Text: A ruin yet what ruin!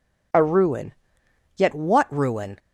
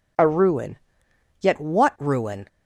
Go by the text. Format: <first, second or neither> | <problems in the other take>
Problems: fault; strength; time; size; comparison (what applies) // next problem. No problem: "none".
neither | pauses between "ruin" and "yet"; noticeable; the same in both